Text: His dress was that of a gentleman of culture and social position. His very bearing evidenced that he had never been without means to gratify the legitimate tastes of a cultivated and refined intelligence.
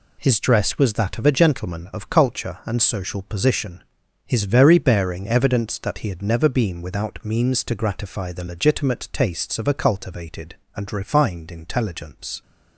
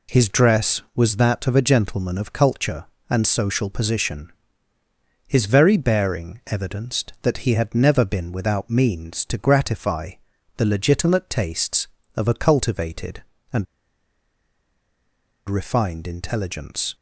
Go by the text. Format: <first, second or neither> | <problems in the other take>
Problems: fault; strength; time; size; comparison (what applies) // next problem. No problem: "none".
first | pauses between "gratify" and "the"; at 10.1 s; 0.42 s long // pauses between "and" and "refined"; strong; at 13.6 s; 1.8 s long